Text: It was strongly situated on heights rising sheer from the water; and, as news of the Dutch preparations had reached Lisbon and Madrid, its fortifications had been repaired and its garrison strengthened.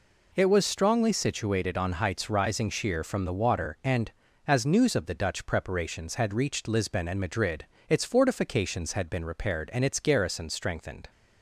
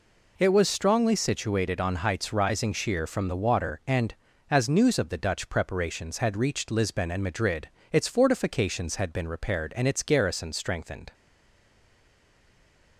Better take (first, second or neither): first